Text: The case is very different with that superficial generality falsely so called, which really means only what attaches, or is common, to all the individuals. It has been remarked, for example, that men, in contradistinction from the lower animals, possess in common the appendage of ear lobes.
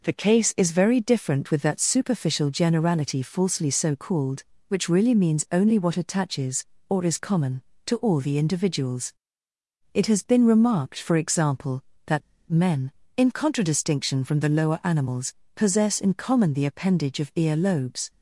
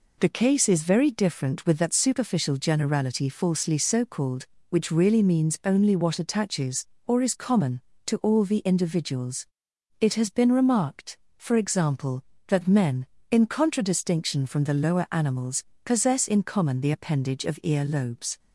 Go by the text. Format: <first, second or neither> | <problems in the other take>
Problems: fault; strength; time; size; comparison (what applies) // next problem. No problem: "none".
second | pauses between "that" and "men"; slight; at 12.2 s; 0.28 s long